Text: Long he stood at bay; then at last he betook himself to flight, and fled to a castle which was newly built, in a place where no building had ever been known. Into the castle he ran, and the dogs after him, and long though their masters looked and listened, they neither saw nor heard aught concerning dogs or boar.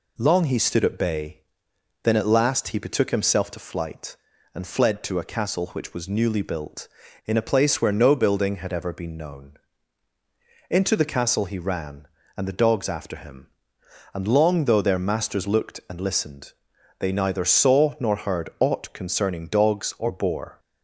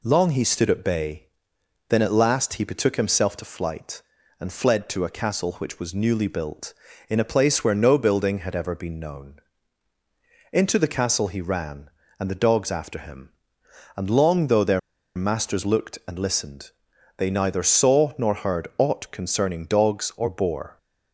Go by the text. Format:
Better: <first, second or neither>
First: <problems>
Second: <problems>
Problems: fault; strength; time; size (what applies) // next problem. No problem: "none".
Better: first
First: none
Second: pauses between "their" and "masters"; at 14.7 s; 0.37 s long